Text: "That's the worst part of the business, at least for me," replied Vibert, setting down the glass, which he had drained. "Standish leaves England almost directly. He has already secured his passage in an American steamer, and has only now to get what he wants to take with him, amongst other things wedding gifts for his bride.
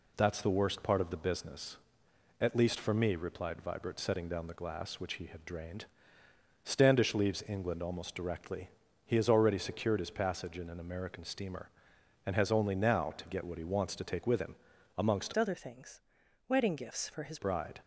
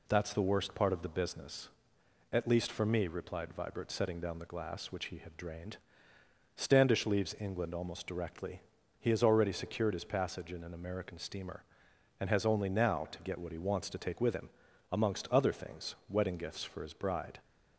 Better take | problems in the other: second | changes voice from "other" to "his"; from 15.3 to 17.3 s; 2.0 s long // pauses between "things" and "wedding"; noticeable; at 16.0 s; 0.48 s long

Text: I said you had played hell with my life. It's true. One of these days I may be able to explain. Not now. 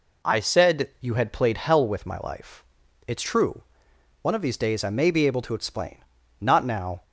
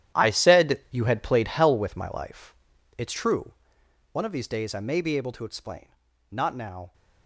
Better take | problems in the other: first | gets quieter; strong; throughout; 13.5 dB

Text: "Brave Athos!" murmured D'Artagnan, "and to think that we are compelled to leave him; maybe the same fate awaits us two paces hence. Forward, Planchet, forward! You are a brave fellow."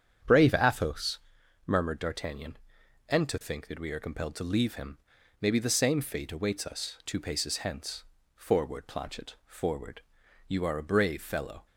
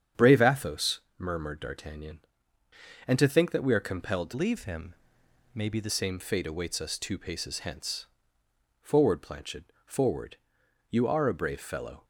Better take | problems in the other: first | starts louder than the rest; strong; until 1.3 s; 8 dB; strong in the first // changes voice from "leave" to "the"; from 4.3 to 5.8 s; 1.5 s long

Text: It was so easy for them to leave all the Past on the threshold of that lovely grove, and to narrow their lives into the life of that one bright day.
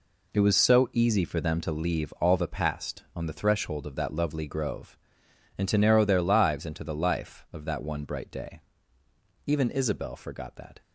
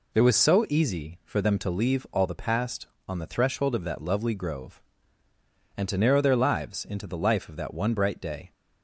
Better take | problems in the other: second | goes on to say "Even Isabel forgot that"; from 9.4 s on; 1.3 s long

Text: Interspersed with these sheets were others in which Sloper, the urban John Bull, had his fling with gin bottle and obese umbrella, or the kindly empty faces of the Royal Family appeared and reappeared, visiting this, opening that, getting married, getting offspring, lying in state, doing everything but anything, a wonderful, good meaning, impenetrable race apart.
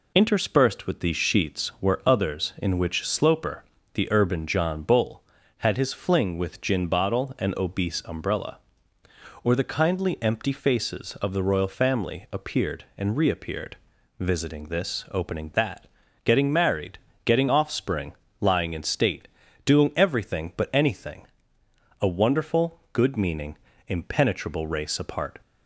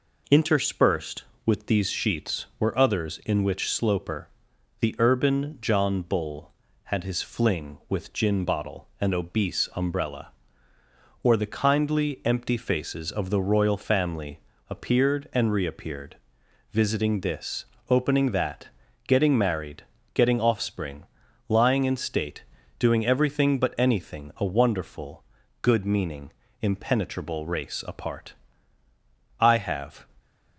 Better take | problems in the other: first | pauses between "Family" and "appeared"; slight; at 14.3 s; 0.32 s long // goes on to say "I have"; noticeable; from 29.3 s on; 0.68 s long

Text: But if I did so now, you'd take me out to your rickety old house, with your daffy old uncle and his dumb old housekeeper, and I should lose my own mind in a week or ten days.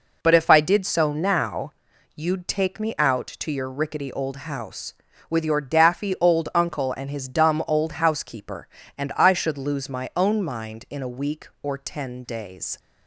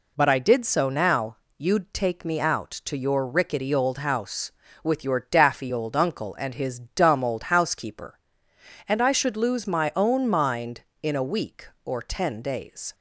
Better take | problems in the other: first | skips "if"; at 0.2 s

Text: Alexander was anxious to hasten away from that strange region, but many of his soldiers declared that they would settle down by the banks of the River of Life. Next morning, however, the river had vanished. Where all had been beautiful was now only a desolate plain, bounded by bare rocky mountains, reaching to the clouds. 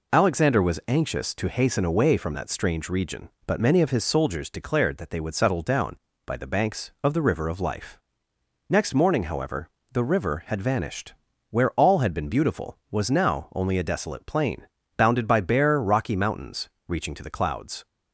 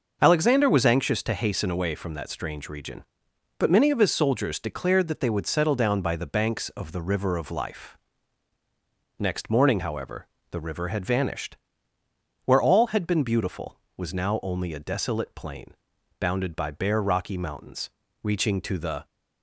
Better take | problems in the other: first | starts louder than the rest; noticeable; until 1.2 s; 6 dB // stops before "clouds"; at 19.0 s

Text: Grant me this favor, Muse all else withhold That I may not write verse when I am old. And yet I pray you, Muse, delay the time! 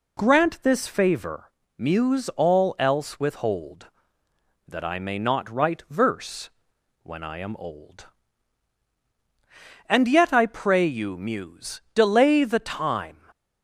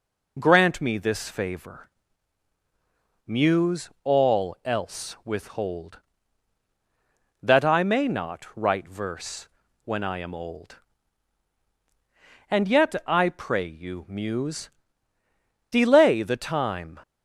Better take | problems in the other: second | skips "me"; at 0.6 s // pauses between "verse" and "when"; noticeable; at 6.4 s; 0.54 s long; slight in the second

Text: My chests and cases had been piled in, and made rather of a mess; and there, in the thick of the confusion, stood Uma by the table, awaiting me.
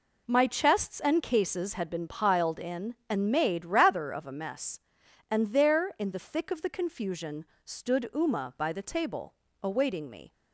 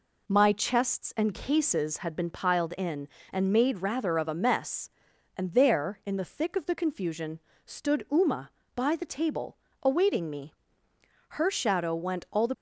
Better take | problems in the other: first | goes on to say "Her shadow went all the"; noticeable; from 11.2 s on; 1.2 s long

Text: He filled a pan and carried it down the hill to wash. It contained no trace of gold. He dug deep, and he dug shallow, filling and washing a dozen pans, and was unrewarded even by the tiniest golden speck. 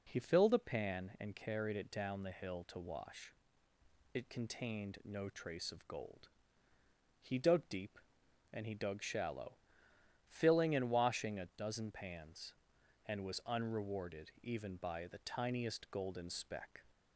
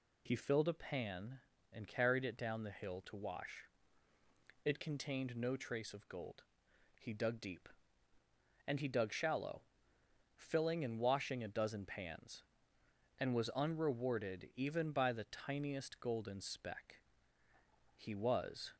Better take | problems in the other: first | goes on to say "He was"; noticeable; from 17.9 s on; 0.78 s long

